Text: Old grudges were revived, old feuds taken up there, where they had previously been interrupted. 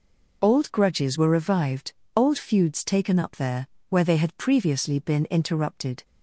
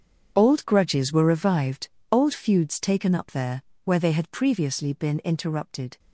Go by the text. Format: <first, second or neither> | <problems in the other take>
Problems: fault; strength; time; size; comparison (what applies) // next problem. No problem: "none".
first | gets quieter; strong; throughout; 14.5 dB